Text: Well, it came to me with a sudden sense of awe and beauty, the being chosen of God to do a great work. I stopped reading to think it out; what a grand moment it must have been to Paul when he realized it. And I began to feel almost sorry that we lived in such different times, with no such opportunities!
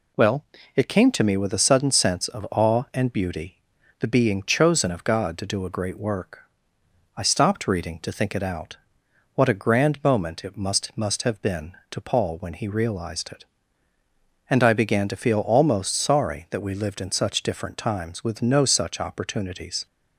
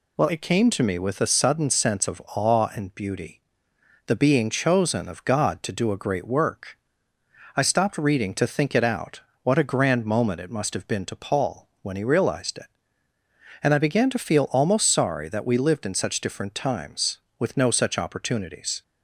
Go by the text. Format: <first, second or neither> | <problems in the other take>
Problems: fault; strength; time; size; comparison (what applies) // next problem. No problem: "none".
second | says "must" twice; at 10.9 s